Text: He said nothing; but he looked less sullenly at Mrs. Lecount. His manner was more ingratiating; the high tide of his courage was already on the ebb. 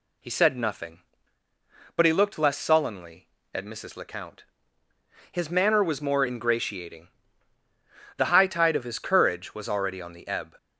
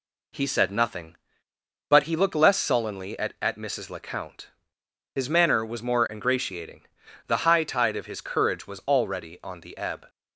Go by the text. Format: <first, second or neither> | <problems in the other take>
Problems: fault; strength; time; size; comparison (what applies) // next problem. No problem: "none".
first | says "at" twice; at 3.3 s